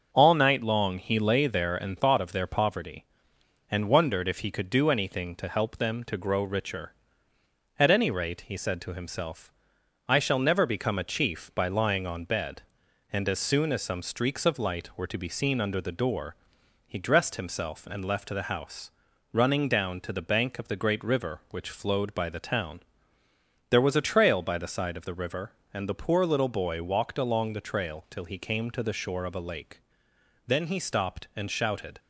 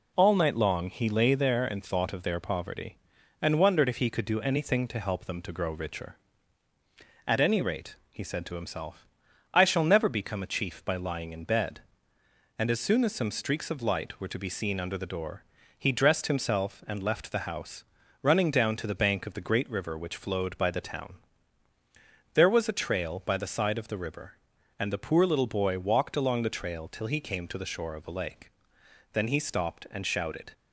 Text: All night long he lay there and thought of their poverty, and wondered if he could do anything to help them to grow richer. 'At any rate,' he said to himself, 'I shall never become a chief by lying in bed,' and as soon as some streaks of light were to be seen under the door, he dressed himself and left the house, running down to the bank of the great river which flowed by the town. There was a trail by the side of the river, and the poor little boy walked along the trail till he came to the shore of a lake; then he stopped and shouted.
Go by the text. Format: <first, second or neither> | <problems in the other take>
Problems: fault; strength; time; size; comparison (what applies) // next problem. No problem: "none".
second | starts louder than the rest; until 1.1 s; 6 dB // says "on" for "in"; at 12.0 s